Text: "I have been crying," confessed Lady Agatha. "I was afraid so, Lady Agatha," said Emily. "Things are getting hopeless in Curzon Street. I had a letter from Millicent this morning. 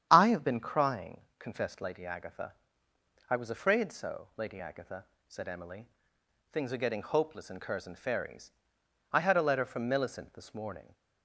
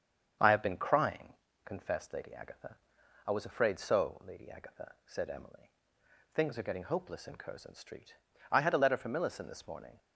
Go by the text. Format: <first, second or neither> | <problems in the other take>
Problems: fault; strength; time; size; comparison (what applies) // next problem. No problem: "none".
second | starts louder than the rest; strong; until 1.1 s; 9 dB; strong in the second // says "Ferries" for "Street"; at 7.9 s